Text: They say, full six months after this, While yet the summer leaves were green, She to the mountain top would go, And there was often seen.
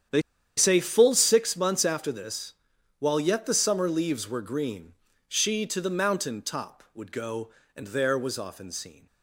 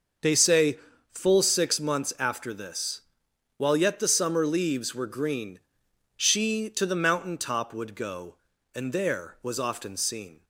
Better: second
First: starts louder than the rest; strong; until 1.4 s; 9 dB // pauses between "They" and "say"; at 0.2 s; 0.36 s long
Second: starts louder than the rest; until 1.5 s; 6 dB

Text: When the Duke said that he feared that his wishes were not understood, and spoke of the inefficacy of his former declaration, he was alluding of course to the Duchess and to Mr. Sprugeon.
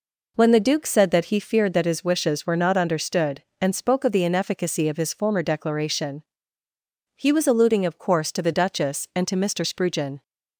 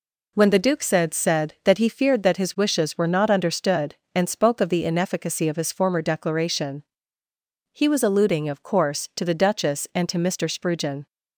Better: first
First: none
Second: says "said" twice; at 1.1 s

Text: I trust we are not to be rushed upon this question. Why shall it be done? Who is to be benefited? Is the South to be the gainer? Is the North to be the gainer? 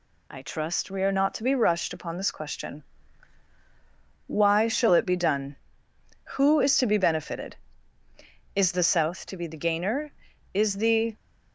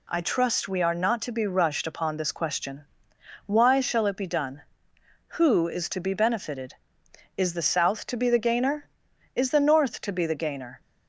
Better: second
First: stops before "North to be the gainer"; at 11.1 s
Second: none

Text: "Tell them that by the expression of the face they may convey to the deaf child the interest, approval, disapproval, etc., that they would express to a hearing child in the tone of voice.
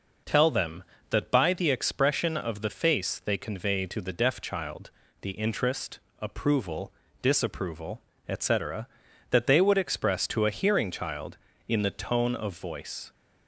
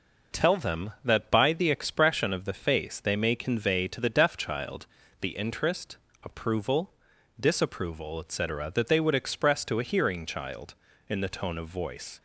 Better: second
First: skips "may"; at 3.3 s // pauses between "child" and "the"; slight; at 4.8 s; 0.32 s long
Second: pauses between "child" and "the"; slight; at 4.8 s; 0.36 s long

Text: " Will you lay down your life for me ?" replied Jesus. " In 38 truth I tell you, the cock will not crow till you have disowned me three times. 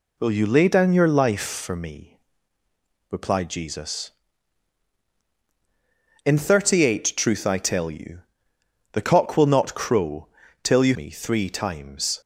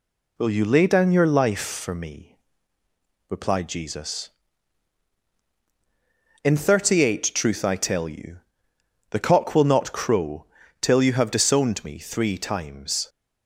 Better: second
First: pauses between "crow" and "till"; at 10.2 s; 0.38 s long // skips "have disowned"; at 10.9 s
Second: pauses between "crow" and "till"; at 10.4 s; 0.38 s long

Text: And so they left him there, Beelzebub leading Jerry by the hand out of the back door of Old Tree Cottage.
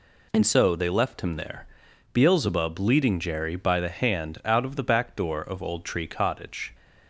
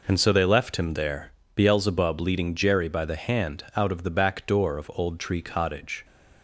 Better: neither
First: none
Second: none

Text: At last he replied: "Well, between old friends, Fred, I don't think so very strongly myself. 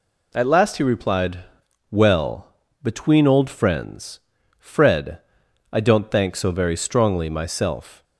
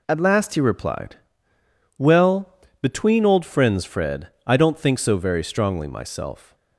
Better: second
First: says "thank" for "think"; at 6.1 s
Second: none

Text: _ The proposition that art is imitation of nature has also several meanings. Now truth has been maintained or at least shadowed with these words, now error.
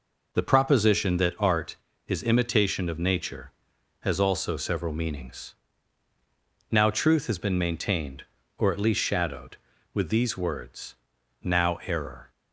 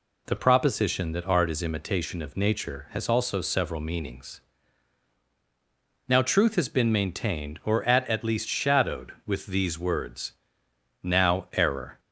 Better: first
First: none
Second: says "at" twice; at 8.0 s

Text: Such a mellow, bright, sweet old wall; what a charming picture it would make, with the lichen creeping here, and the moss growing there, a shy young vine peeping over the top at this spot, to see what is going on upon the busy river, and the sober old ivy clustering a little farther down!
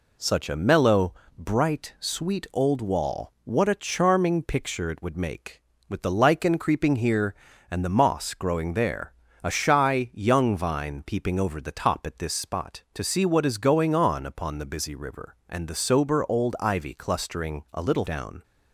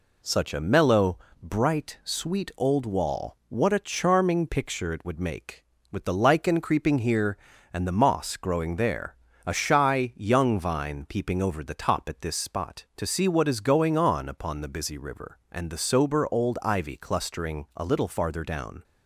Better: second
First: skips "farther"; at 18.0 s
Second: none

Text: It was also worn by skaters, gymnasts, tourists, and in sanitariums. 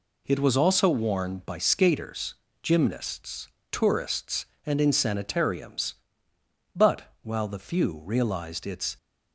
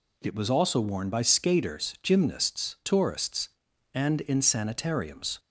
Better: second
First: goes on to say "But while the few realized its"; strong; from 6.7 s on; 2.2 s long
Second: none

